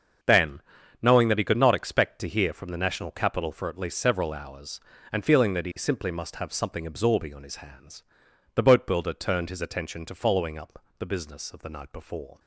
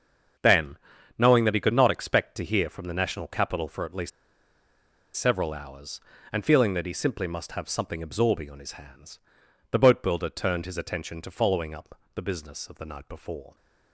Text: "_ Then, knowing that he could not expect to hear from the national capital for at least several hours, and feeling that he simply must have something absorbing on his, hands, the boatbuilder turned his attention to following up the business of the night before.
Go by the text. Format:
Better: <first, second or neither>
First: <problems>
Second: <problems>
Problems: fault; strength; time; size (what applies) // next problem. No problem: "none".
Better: first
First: starts louder than the rest; until 1.6 s; 7 dB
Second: starts louder than the rest; until 1.8 s; 7 dB // pauses between "least" and "several"; at 4.1 s; 1.0 s long